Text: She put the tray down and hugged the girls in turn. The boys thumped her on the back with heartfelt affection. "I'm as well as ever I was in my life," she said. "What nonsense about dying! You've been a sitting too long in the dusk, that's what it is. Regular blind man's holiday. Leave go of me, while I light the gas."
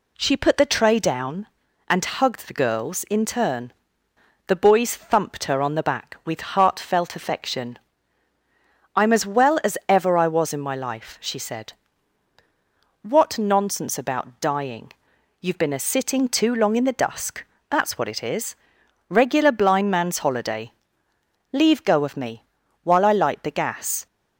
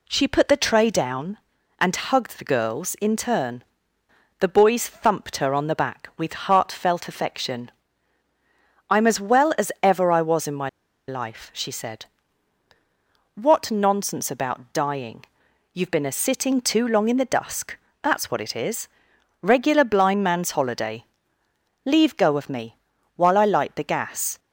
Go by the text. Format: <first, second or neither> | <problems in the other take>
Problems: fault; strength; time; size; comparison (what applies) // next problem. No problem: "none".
first | pauses between "my" and "life"; at 10.6 s; 0.39 s long